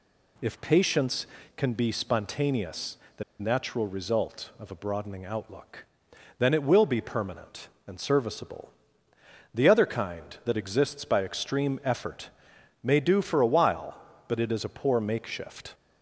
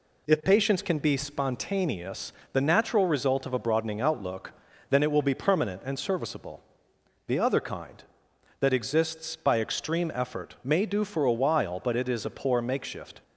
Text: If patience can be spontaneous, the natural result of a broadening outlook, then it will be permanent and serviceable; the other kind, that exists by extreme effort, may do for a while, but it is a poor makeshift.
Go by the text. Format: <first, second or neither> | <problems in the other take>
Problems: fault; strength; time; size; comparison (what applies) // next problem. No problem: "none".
second | pauses between "the" and "natural"; slight; at 3.2 s; 0.17 s long